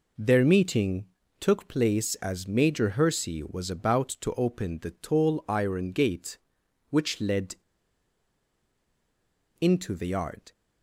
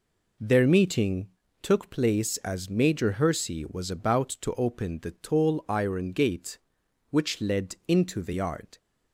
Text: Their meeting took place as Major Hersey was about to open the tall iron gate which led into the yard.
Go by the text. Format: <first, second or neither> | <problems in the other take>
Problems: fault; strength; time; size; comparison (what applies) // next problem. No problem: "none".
second | pauses between "meeting" and "took"; slight; at 1.0 s; 0.34 s long; slight in the second // pauses between "led" and "into"; strong; at 7.5 s; 2.0 s long